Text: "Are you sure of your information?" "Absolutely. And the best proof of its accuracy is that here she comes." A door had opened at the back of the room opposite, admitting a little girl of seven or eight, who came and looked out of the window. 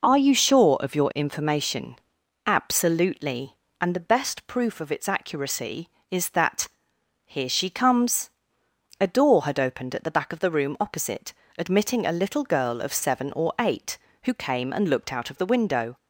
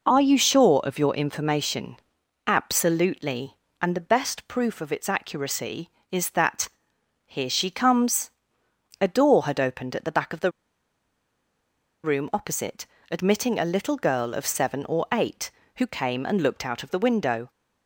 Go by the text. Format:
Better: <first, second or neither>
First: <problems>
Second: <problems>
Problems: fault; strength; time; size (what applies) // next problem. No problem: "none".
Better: first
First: pauses between "that" and "here"; noticeable; at 6.6 s; 0.56 s long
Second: pauses between "that" and "here"; noticeable; at 6.6 s; 0.56 s long // pauses between "the" and "room"; strong; at 10.5 s; 1.5 s long